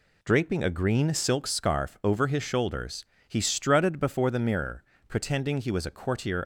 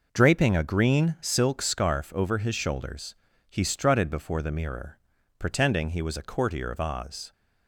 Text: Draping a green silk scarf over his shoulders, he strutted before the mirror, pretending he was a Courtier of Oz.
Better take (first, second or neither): second